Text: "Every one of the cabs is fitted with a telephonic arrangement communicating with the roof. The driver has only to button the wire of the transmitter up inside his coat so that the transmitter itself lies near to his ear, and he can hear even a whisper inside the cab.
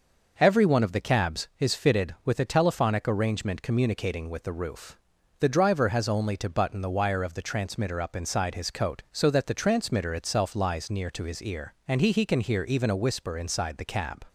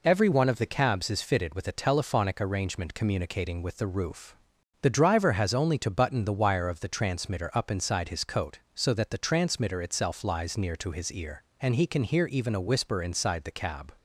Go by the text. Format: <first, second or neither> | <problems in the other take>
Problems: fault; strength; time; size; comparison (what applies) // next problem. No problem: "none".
second | says "he" twice; at 12.1 s